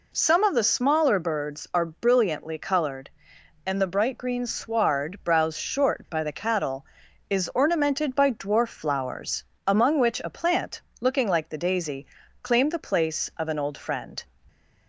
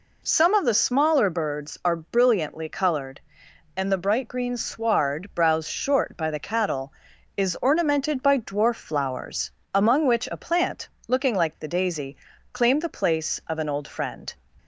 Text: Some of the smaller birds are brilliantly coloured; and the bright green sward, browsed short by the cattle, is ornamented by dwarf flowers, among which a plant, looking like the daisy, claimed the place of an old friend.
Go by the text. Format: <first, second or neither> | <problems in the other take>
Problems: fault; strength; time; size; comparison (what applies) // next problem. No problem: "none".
neither | none